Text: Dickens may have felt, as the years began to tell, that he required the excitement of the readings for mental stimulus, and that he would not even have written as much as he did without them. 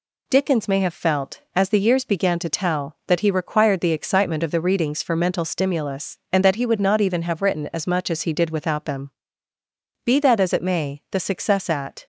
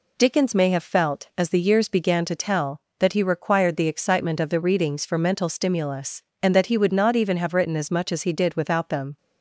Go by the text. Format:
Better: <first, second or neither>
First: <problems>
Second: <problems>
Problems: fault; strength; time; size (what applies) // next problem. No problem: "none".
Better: second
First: goes on to say "Be that as it may the success at"; strong; from 10.0 s on; 2.0 s long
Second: none